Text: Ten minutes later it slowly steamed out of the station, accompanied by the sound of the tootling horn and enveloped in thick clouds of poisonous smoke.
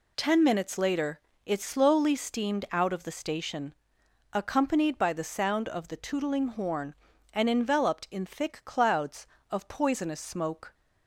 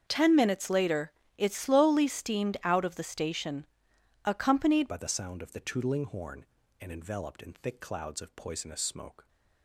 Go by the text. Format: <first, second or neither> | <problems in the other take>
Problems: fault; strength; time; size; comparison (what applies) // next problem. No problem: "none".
first | starts louder than the rest; strong; until 1.0 s; 7 dB // pauses between "later" and "it"; slight; at 1.1 s; 0.26 s long; slight in the first // changes voice at "by"; from 4.8 s on; 4.4 s long